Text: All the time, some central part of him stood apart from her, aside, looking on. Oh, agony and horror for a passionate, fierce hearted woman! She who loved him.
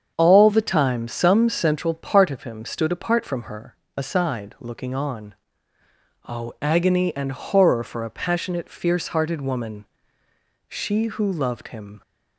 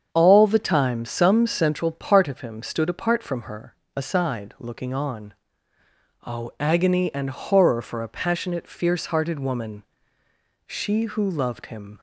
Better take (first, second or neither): neither